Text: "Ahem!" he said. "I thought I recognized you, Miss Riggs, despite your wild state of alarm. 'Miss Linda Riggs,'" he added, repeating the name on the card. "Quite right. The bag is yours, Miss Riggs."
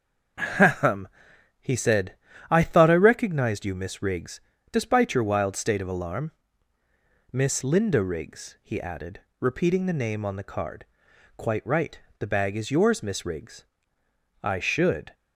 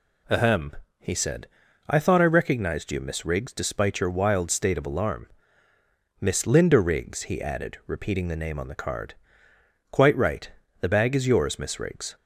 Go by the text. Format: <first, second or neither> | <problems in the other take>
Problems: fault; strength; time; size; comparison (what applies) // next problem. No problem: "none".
second | starts louder than the rest; until 1.8 s; 6 dB // goes on to say "I should"; noticeable; from 14.4 s on; 0.70 s long